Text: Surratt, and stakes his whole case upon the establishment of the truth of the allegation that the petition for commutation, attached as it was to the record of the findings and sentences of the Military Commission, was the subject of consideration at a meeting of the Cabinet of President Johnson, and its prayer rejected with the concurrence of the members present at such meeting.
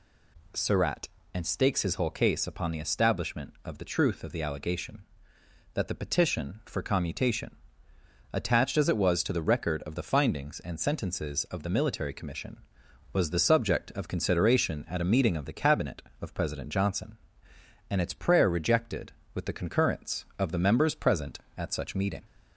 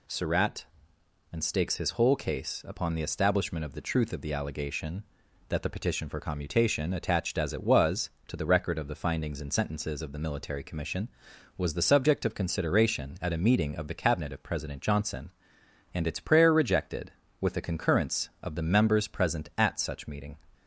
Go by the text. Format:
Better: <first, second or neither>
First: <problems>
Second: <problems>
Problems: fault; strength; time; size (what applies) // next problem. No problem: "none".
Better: neither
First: none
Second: none